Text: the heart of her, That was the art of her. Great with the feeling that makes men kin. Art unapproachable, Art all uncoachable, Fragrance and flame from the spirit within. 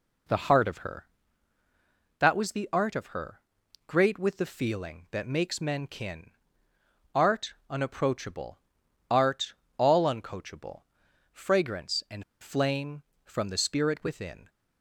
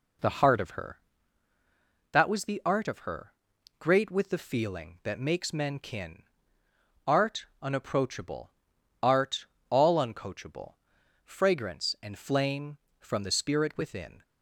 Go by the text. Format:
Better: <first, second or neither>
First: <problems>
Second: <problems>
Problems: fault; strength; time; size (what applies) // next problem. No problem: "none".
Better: second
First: pauses between "Art" and "unapproachable"; slight; at 7.5 s; 0.16 s long // pauses between "Art" and "all"; slight; at 9.5 s; 0.24 s long // pauses between "and" and "flame"; slight; at 12.2 s; 0.19 s long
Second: pauses between "Art" and "unapproachable"; slight; at 7.4 s; 0.16 s long // pauses between "Art" and "all"; slight; at 9.4 s; 0.24 s long